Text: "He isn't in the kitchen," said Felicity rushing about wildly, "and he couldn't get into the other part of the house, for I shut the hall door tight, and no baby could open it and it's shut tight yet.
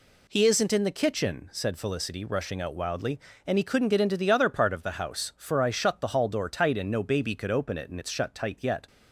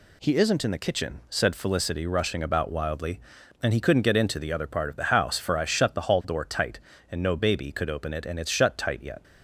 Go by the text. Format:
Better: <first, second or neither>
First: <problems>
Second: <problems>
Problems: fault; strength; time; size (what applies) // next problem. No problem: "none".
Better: second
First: says "out" for "about"; at 2.6 s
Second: none